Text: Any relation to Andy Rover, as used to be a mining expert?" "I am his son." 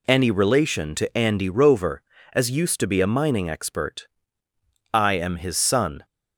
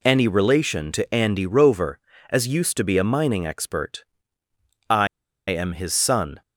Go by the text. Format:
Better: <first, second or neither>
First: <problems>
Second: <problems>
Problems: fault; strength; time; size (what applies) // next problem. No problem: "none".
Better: first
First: none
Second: pauses between "I" and "am"; at 5.0 s; 0.41 s long